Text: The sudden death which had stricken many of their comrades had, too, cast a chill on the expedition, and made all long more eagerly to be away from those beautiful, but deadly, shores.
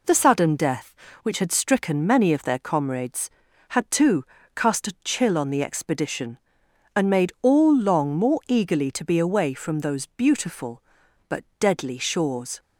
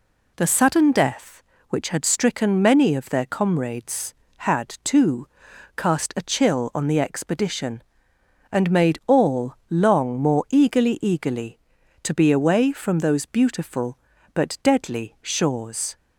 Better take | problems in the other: first | pauses between "all" and "long"; slight; at 9.5 s; 0.16 s long // says "eagerly" twice; at 11.0 s

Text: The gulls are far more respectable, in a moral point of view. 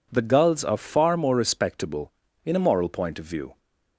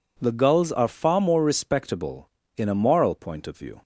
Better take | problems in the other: neither | none

